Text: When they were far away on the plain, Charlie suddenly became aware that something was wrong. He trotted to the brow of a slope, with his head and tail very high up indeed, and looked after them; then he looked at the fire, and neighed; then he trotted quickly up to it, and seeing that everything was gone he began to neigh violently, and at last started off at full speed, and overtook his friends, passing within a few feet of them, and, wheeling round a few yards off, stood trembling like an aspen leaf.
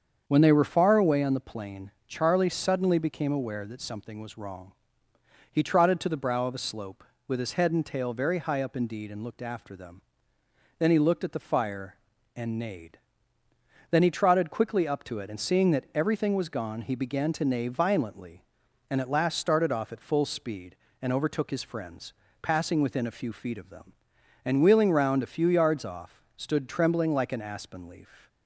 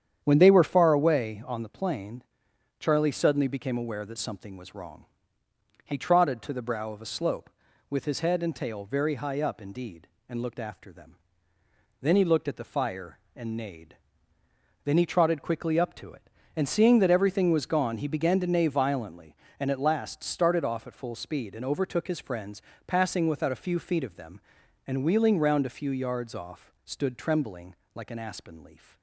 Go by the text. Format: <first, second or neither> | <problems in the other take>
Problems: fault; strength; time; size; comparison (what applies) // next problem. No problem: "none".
first | starts louder than the rest; strong; until 1.2 s; 9 dB; strong in the first // says "without" for "within"; at 23.2 s // pauses between "trembling" and "like"; slight; at 27.7 s; 0.18 s long